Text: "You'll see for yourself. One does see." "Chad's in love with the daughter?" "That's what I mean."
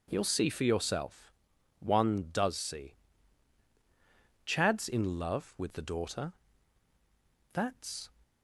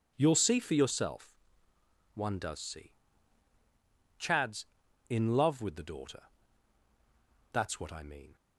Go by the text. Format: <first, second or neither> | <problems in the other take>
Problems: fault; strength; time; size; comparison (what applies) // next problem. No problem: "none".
second | stops before "what I mean"; at 8.2 s